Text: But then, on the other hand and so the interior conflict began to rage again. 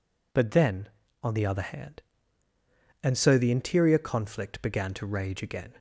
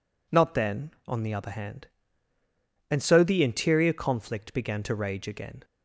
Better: first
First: none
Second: says "Not" for "But"; at 0.2 s

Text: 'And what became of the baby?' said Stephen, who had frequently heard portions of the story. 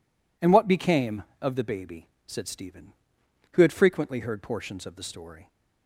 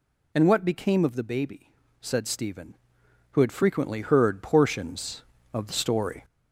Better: first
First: none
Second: gets louder; slight; throughout; 2.5 dB

